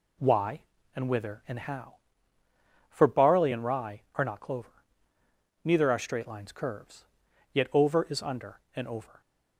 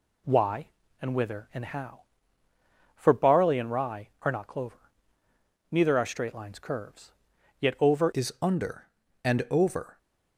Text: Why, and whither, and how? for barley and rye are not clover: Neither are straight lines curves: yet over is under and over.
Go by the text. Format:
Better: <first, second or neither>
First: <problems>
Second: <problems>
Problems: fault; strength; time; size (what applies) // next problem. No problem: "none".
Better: first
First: none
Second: changes voice at "is"; from 8.1 s on; 1.8 s long